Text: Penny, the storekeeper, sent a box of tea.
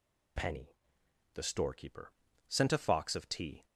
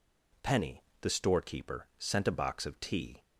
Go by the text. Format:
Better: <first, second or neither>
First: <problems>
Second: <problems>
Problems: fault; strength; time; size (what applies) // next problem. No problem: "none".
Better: second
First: says "fox" for "box"; at 2.7 s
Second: none